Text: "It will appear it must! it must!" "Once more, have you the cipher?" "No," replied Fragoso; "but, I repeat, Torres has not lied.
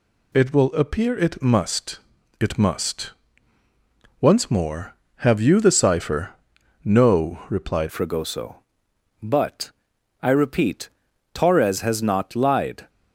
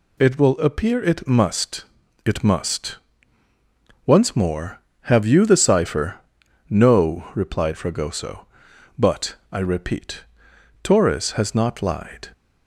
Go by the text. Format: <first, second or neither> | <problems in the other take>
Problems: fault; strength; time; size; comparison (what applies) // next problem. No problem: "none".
second | changes voice at "Fragoso"; from 7.9 s on; 4.9 s long